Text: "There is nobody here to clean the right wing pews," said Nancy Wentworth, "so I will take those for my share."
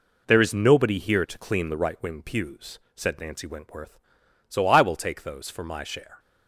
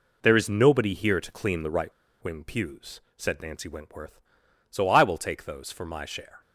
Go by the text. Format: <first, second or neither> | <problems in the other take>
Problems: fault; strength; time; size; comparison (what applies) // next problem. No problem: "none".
first | pauses between "right" and "wing"; slight; at 1.9 s; 0.30 s long